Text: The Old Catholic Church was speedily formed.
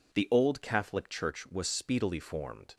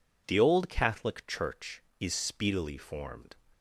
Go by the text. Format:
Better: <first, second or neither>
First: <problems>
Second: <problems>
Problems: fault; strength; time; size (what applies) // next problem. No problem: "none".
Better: first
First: none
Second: says "is" for "was"; at 2.0 s